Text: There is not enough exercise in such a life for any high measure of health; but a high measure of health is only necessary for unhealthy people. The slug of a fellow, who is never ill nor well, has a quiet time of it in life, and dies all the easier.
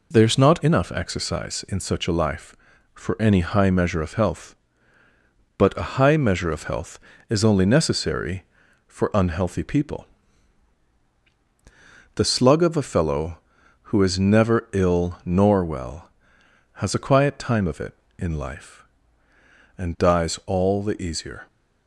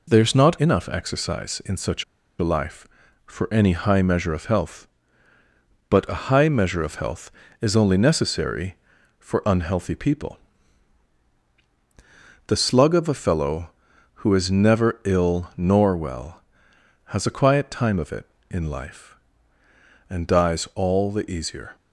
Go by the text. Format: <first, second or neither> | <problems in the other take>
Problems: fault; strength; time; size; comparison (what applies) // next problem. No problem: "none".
first | pauses between "such" and "a"; at 2.0 s; 0.36 s long